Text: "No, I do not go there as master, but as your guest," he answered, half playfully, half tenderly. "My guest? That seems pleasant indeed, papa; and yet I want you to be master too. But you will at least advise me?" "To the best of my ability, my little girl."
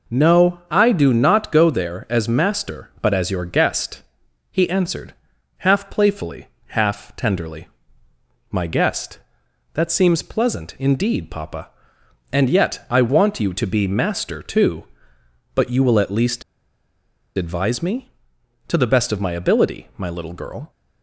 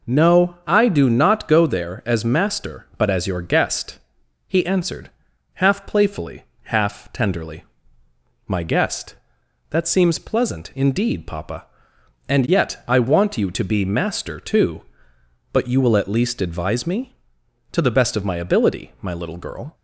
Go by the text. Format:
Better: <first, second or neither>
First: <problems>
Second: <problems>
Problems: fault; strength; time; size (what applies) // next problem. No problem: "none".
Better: second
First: pauses between "least" and "advise"; noticeable; at 16.4 s; 0.95 s long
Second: none